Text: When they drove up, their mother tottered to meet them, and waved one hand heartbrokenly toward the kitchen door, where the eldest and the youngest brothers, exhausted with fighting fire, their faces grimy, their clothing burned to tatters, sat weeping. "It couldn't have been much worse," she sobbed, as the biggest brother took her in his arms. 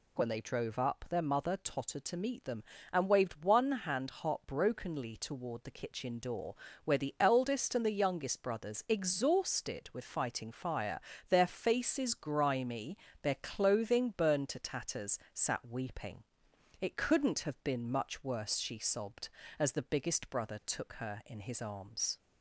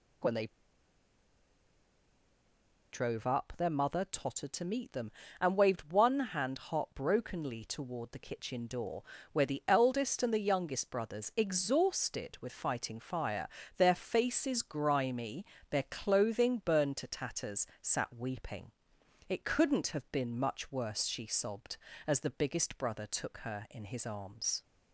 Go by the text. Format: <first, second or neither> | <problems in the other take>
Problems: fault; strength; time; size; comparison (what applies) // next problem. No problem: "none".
first | pauses between "they" and "drove"; strong; at 0.4 s; 2.4 s long